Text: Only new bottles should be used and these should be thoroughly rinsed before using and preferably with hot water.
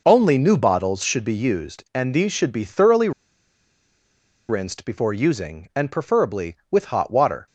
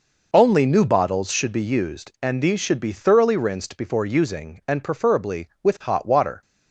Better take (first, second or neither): second